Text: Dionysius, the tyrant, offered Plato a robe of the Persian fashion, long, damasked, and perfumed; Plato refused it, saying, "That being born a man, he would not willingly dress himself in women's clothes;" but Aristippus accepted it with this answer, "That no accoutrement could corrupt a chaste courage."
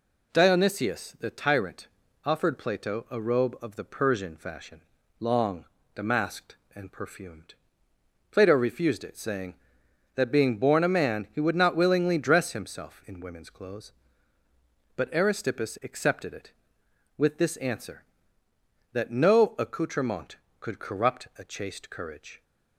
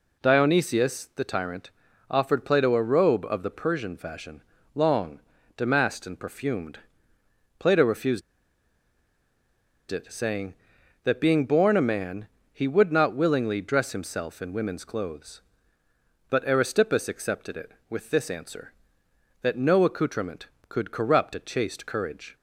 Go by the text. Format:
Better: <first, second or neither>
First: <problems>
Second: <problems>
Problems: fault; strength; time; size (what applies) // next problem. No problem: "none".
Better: first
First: none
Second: pauses between "refused" and "it"; strong; at 8.2 s; 1.6 s long